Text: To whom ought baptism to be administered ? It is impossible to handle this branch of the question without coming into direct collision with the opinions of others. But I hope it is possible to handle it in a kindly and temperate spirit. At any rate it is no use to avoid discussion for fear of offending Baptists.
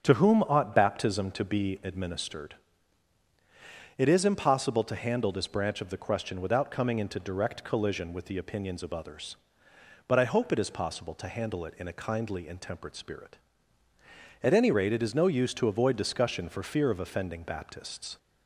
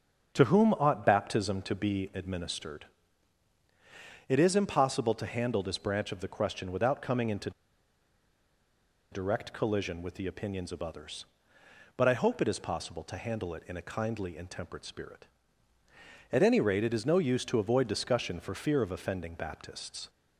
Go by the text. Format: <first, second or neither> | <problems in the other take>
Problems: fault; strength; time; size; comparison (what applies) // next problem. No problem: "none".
first | starts louder than the rest; strong; until 1.3 s; 7.5 dB; strong in the first // pauses between "into" and "direct"; strong; at 7.5 s; 1.6 s long